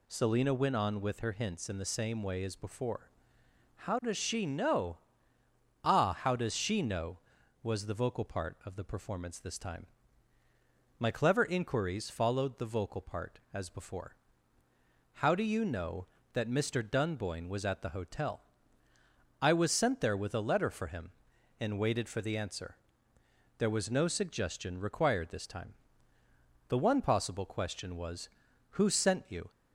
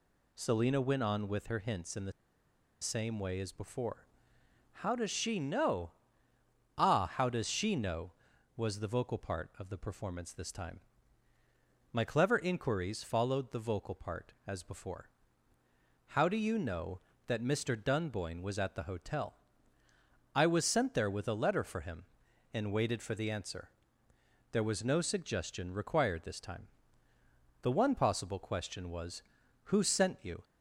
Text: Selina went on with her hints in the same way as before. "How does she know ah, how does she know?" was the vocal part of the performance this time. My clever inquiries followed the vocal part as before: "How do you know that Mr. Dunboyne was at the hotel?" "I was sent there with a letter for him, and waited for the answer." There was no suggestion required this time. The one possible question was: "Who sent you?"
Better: first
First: pauses between "know" and "ah"; noticeable; at 4.9 s; 0.86 s long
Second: pauses between "the" and "same"; noticeable; at 2.1 s; 0.69 s long // pauses between "know" and "ah"; noticeable; at 5.9 s; 0.86 s long

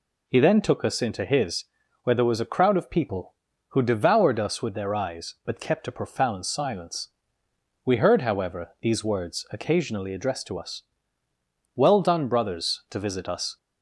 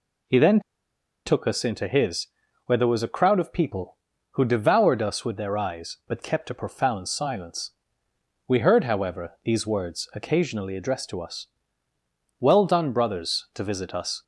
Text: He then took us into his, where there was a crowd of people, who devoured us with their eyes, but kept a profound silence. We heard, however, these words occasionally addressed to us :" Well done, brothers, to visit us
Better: first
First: none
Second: pauses between "then" and "took"; noticeable; at 0.5 s; 0.66 s long

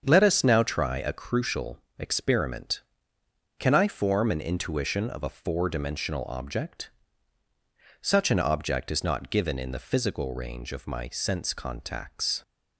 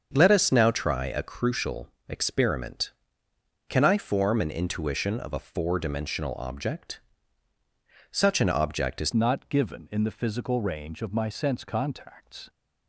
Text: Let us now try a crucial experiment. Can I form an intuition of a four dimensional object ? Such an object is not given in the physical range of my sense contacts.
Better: first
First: starts louder than the rest; until 1.0 s; 7 dB // pauses between "crucial" and "experiment"; slight; at 1.7 s; 0.18 s long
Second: starts louder than the rest; until 1.1 s; 7 dB // pauses between "crucial" and "experiment"; slight; at 1.8 s; 0.18 s long // changes voice at "not"; from 9.1 s on; 3.3 s long

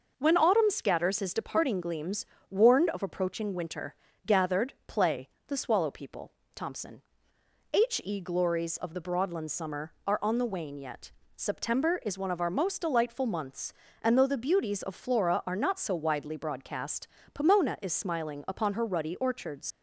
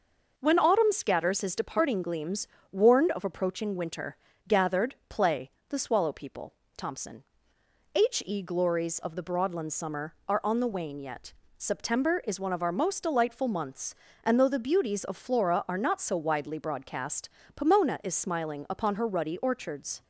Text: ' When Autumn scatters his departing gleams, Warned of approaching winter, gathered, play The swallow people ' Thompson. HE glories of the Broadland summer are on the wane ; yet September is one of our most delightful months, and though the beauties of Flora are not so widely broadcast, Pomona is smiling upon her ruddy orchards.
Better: second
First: pauses between "play" and "The"; slight; at 5.2 s; 0.20 s long // pauses between "yet" and "September"; slight; at 11.1 s; 0.24 s long // leaves "orchards" unfinished; at 19.7 s; 110 ms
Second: pauses between "play" and "The"; slight; at 5.4 s; 0.20 s long // pauses between "yet" and "September"; slight; at 11.3 s; 0.24 s long

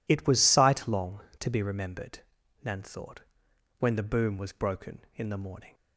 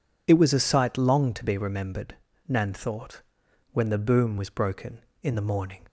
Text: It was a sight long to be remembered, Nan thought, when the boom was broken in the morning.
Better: second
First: skips "a"; at 0.4 s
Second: none

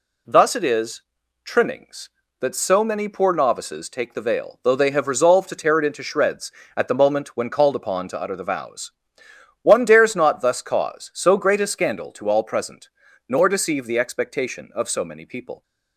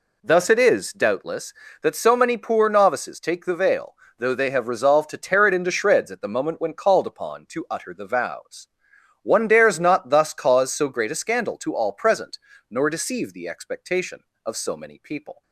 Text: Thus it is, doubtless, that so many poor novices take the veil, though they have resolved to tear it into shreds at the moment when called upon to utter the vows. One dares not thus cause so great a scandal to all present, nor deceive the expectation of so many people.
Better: second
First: says "trimmings" for "doubtless"; at 1.4 s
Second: none

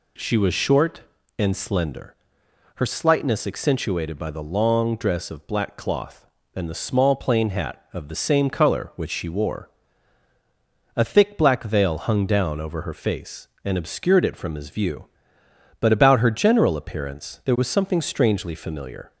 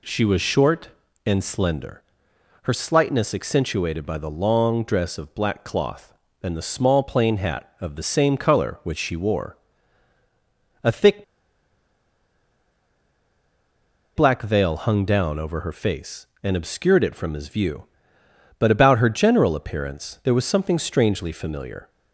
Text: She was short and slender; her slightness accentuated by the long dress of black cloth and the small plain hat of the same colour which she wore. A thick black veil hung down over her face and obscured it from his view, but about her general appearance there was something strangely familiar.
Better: first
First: none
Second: pauses between "thick" and "black"; strong; at 11.2 s; 2.9 s long

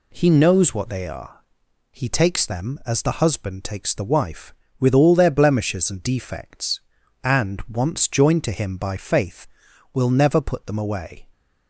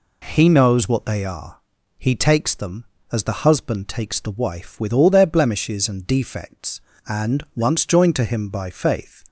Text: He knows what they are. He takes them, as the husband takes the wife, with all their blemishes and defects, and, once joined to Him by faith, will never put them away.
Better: first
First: none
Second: stops before "will never put them away"; at 9.2 s

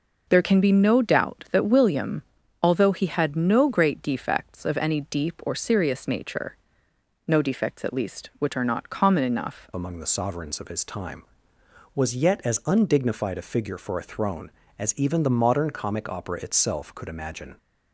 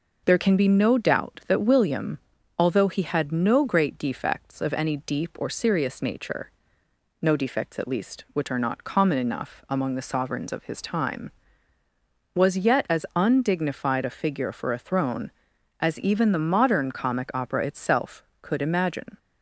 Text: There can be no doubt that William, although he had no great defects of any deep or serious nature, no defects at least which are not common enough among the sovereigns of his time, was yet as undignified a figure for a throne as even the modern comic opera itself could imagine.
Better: second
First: changes voice at "among"; from 9.7 s on; 7.8 s long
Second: none

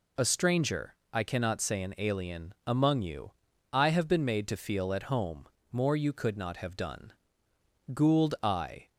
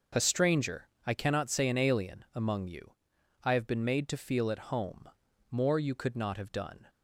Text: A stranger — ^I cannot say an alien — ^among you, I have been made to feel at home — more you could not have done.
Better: second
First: goes on to say "Gould I"; noticeable; from 7.9 s on; 0.96 s long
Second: none

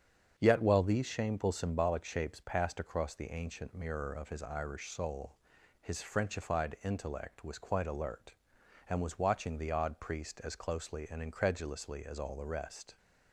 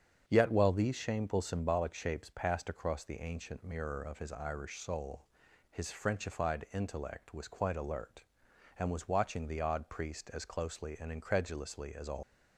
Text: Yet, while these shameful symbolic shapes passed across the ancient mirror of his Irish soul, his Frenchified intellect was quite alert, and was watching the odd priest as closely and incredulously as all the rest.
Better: first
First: starts louder than the rest; strong; until 1.3 s; 7.5 dB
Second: starts louder than the rest; strong; until 1.2 s; 7.5 dB // stops before "the rest"; at 12.2 s

